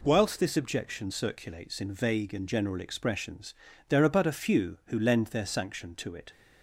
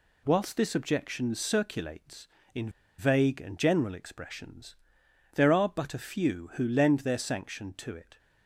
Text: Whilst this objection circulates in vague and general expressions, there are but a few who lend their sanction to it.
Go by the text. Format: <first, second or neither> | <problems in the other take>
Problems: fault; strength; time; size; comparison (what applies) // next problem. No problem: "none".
first | pauses between "in" and "vague"; slight; at 2.6 s; 0.28 s long